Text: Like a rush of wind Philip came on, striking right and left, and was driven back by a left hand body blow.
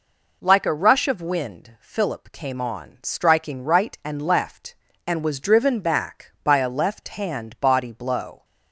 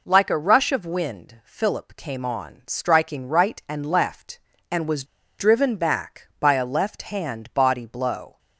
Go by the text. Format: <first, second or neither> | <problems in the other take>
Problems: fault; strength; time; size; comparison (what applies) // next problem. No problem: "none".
first | pauses between "was" and "driven"; slight; at 5.0 s; 0.34 s long